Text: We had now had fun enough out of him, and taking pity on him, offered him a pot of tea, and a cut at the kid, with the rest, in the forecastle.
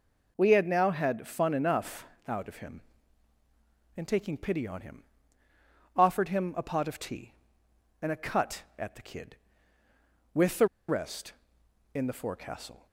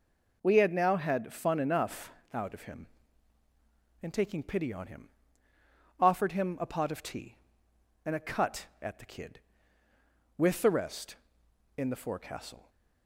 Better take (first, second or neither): second